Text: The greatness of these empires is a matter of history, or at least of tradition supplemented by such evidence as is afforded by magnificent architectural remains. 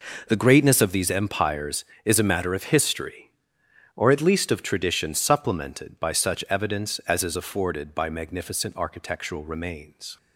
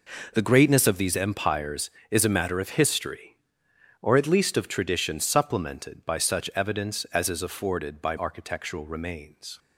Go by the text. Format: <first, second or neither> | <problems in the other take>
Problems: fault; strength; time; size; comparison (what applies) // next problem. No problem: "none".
first | skips "magnificent"; at 8.1 s